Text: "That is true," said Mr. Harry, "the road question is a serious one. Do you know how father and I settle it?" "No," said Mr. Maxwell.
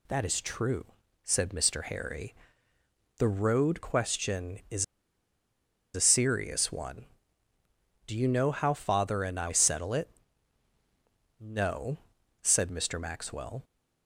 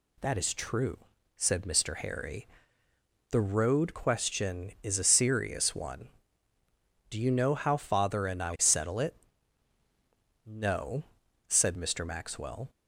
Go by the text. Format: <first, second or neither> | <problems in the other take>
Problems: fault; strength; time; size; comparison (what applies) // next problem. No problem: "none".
second | pauses between "is" and "a"; at 4.8 s; 1.1 s long